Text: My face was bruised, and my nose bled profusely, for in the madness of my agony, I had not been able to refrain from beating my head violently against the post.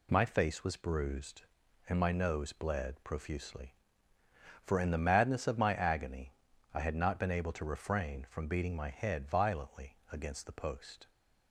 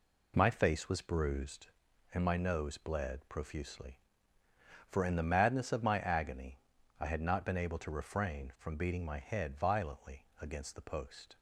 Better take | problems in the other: first | starts louder than the rest; slight; until 1.7 s; 3 dB

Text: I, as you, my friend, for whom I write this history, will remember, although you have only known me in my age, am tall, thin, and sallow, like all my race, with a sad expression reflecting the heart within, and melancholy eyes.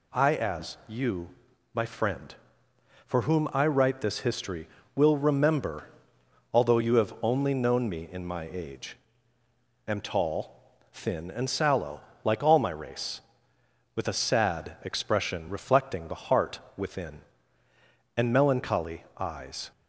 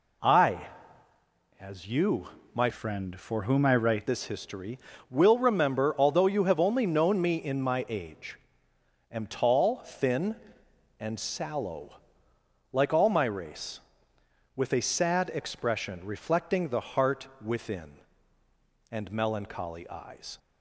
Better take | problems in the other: first | changes voice from "friend" to "write"; from 2.7 to 4.0 s; 1.3 s long // pauses between "heart" and "within"; slight; at 17.2 s; 0.16 s long; slight in the first

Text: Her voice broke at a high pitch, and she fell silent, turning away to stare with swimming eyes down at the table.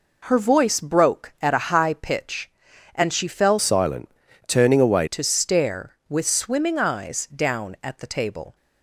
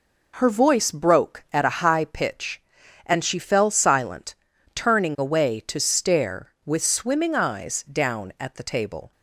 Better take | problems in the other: second | changes voice from "silent" to "away"; from 3.5 to 5.0 s; 1.5 s long

